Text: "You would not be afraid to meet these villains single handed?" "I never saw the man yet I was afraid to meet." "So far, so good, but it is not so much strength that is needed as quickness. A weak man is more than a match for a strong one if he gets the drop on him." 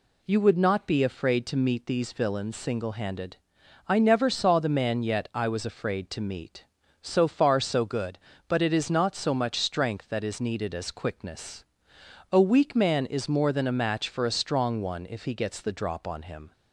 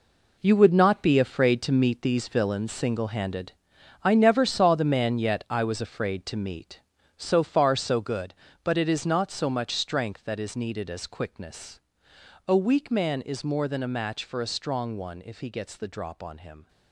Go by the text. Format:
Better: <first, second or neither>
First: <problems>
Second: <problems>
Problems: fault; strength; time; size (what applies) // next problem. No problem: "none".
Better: first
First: none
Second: gets quieter; strong; throughout; 11 dB